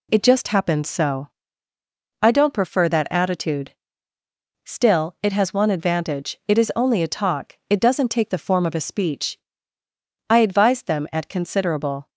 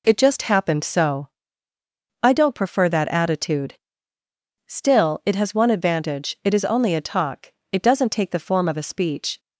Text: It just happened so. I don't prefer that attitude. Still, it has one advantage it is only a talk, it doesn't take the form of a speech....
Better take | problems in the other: second | goes on to say "I advised them at considerable"; strong; from 10.3 s on; 1.7 s long

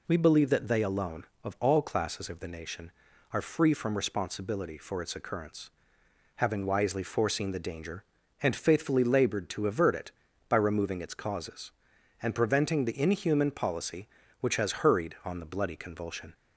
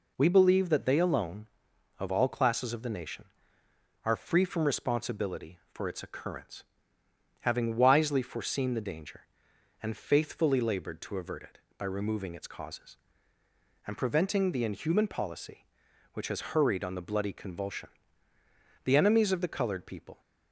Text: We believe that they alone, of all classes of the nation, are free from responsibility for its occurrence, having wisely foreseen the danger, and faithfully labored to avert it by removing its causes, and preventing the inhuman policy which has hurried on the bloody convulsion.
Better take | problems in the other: first | goes on to say "The enemies of the colored people"; from 18.8 s on; 1.3 s long

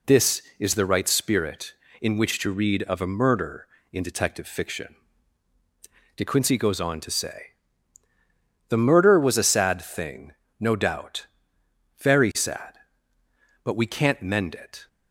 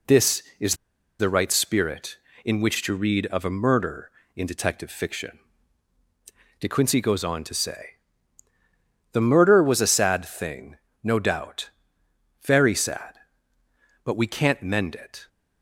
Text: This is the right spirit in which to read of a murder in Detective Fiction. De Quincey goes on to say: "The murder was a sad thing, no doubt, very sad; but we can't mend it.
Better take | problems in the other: first | pauses between "is" and "the"; at 0.7 s; 0.44 s long

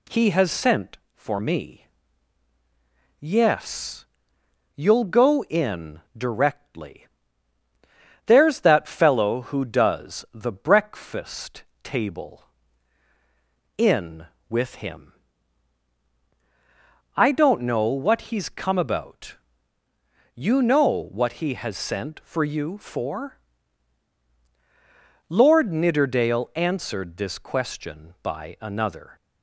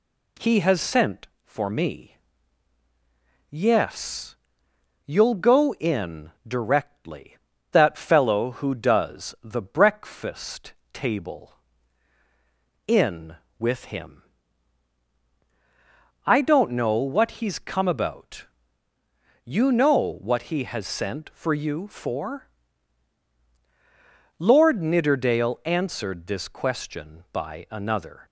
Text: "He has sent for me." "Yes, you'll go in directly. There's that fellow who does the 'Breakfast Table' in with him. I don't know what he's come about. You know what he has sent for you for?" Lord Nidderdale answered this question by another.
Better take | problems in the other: first | skips "There's"; at 7.5 s // pauses between "Breakfast" and "Table"; slight; at 10.7 s; 0.20 s long; slight in the first

